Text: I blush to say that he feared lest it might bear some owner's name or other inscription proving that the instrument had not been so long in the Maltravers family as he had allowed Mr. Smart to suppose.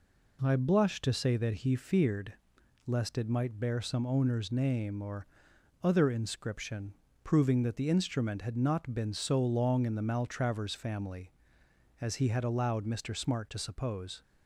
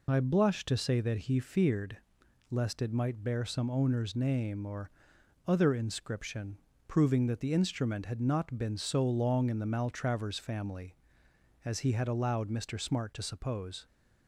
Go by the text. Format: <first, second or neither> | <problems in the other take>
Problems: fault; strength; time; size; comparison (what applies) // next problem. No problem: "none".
first | loses the start of "I"; at 0.0 s; 55 ms // pauses between "feared" and "lest"; noticeable; at 1.9 s; 0.52 s long; noticeable in the first // pauses between "or" and "other"; noticeable; at 4.8 s; 0.58 s long; noticeable in the first // pauses between "inscription" and "proving"; slight; at 6.5 s; 0.30 s long; slight in the first